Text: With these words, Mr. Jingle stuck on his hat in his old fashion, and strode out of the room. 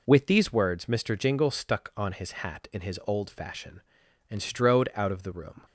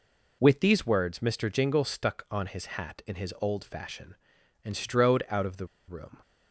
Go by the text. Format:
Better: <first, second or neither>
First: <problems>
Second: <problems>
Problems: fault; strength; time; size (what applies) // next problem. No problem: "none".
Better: first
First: none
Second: pauses between "the" and "room"; slight; at 5.6 s; 0.21 s long